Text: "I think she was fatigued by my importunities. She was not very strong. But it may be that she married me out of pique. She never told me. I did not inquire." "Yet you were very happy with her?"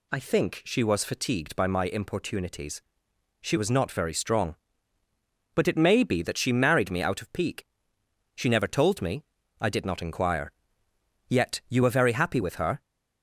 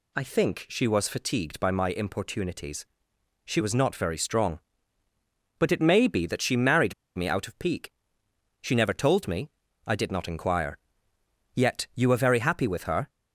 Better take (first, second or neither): first